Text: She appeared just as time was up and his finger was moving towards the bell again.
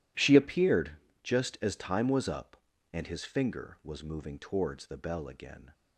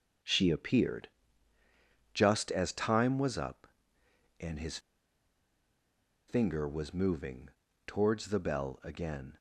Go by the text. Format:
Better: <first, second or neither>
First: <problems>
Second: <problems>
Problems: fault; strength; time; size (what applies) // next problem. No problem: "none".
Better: first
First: pauses between "appeared" and "just"; slight; at 0.9 s; 0.32 s long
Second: starts louder than the rest; until 2.2 s; 6.5 dB // pauses between "appeared" and "just"; at 1.0 s; 1.0 s long // pauses between "his" and "finger"; strong; at 4.7 s; 1.5 s long // pauses between "moving" and "towards"; at 7.4 s; 0.38 s long